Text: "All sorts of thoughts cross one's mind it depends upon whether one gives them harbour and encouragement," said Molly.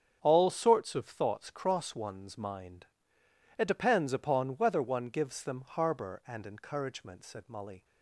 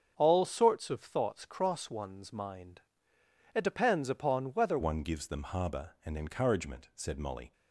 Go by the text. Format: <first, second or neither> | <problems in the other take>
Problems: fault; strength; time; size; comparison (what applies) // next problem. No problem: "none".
first | starts louder than the rest; strong; until 1.1 s; 7.5 dB; strong in the first // pauses between "mind" and "it"; noticeable; at 2.8 s; 0.74 s long; noticeable in the first // changes voice at "one"; from 4.8 s on; 2.7 s long